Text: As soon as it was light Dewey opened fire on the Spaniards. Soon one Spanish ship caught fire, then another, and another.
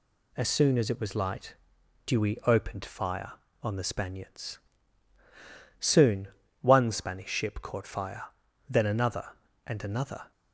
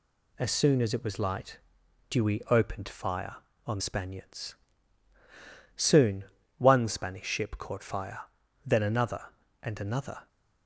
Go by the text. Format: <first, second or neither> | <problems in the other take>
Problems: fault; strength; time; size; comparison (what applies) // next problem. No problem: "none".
first | pauses between "light" and "Dewey"; noticeable; at 1.5 s; 0.50 s long; noticeable in the first // skips "the"; at 3.7 s // pauses between "Soon" and "one"; slight; at 6.2 s; 0.32 s long; slight in the first